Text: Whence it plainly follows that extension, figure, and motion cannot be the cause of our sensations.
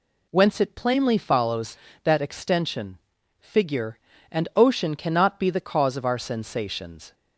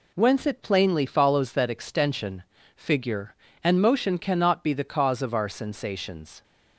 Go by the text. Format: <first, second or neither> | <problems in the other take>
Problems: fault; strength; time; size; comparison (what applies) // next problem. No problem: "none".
second | says "ocean" for "motion"; at 4.5 s